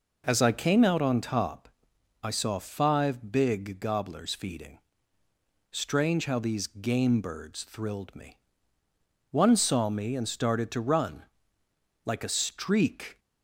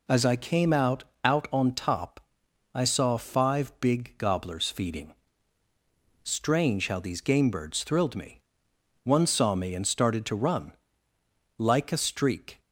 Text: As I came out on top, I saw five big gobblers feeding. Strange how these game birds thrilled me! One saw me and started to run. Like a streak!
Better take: first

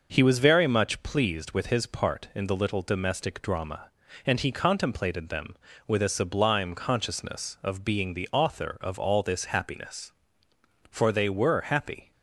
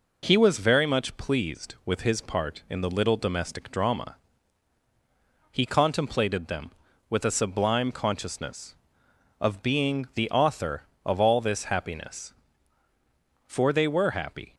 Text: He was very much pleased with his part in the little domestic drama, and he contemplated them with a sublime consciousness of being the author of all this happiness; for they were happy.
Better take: first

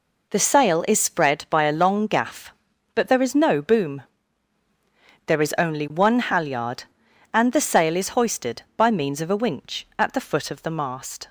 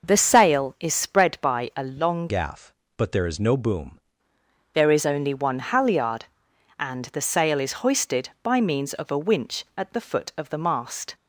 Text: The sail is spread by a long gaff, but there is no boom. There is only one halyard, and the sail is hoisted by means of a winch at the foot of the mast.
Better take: first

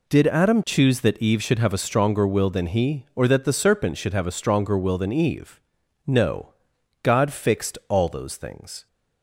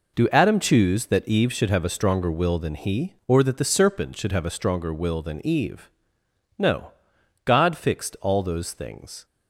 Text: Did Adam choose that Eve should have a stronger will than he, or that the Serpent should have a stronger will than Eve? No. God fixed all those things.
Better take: first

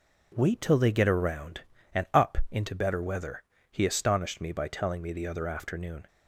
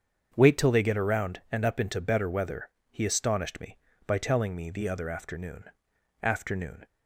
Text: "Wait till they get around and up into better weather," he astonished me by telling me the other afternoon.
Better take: first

